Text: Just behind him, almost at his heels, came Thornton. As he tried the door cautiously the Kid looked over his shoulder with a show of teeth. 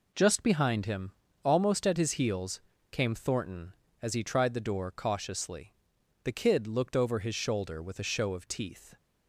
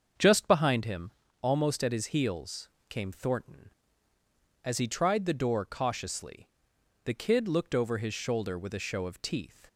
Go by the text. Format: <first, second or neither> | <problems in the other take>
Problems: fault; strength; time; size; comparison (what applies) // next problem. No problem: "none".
first | starts louder than the rest; until 1.4 s; 7 dB // pauses between "cautiously" and "the"; noticeable; at 6.4 s; 0.56 s long; noticeable in the first